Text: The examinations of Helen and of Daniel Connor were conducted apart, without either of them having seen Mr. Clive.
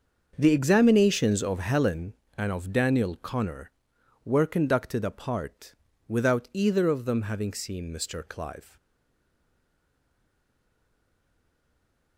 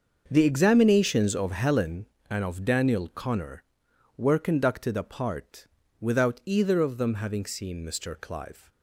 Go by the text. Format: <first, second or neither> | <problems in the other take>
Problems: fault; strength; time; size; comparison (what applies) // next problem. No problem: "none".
second | starts louder than the rest; until 1.3 s; 6.5 dB; also in the second // stays silent after the last word; strong; from 8.7 s on; 3.4 s long